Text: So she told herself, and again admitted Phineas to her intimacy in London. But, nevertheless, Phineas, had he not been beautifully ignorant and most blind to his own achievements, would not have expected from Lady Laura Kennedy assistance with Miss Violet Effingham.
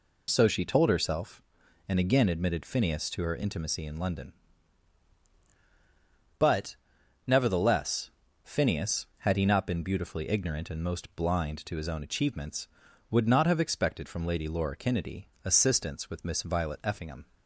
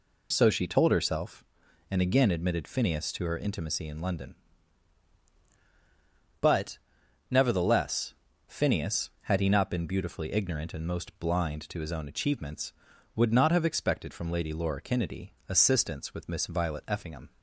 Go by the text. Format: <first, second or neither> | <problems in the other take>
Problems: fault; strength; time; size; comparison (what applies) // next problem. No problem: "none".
neither | pauses between "Kennedy" and "assistance"; slight; the same in both